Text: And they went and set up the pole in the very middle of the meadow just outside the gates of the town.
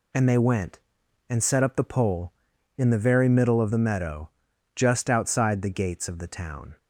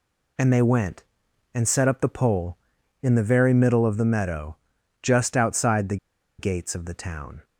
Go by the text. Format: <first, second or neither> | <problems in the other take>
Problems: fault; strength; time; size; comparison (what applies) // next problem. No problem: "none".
first | pauses between "meadow" and "just"; noticeable; at 4.5 s; 0.46 s long; noticeable in the first // pauses between "the" and "gates"; at 5.9 s; 0.42 s long